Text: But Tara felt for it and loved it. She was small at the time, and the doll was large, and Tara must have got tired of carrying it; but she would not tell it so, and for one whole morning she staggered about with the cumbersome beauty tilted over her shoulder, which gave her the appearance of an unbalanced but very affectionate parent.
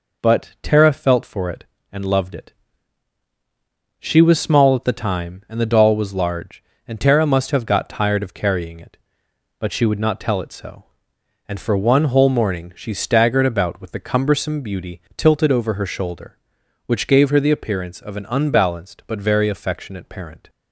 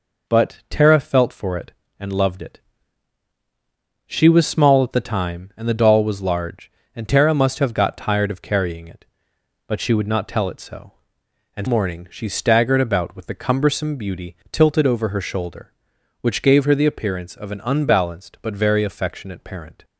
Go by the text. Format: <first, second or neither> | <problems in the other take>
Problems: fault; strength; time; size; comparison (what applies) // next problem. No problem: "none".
first | skips "for one whole"; at 11.6 s // pauses between "beauty" and "tilted"; slight; at 14.3 s; 0.16 s long; slight in the first